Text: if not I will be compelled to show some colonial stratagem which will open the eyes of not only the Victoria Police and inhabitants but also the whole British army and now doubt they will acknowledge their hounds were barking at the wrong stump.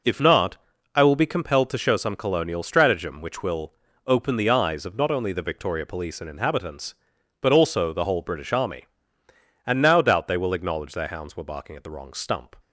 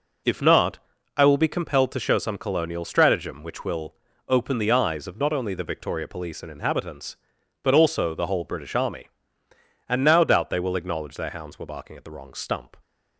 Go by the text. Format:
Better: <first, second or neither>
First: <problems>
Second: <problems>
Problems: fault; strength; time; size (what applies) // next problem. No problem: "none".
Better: neither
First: pauses between "not" and "I"; at 0.5 s; 0.38 s long // pauses between "will" and "open"; slight; at 3.7 s; 0.34 s long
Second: pauses between "not" and "I"; at 0.7 s; 0.38 s long // pauses between "will" and "open"; slight; at 3.9 s; 0.34 s long